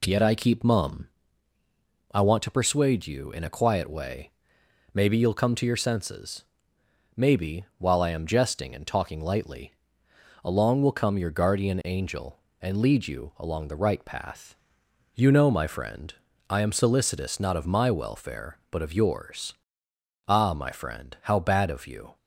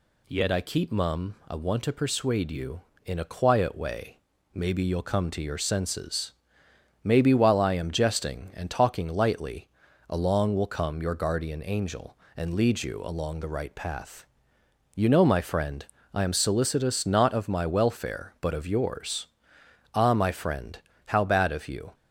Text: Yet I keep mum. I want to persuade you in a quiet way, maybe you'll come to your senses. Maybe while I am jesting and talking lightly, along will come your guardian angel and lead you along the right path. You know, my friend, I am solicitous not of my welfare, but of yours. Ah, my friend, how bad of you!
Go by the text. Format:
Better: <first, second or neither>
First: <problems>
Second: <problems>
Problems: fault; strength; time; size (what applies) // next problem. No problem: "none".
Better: neither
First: none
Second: none